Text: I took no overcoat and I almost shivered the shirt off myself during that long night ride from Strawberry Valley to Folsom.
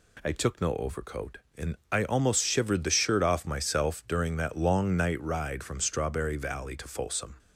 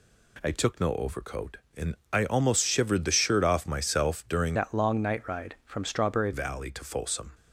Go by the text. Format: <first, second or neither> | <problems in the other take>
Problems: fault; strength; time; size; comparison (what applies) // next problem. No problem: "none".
first | pauses between "and" and "I"; slight; at 1.9 s; 0.18 s long; slight in the first // changes voice from "that" to "Strawberry"; from 4.5 to 6.3 s; 1.8 s long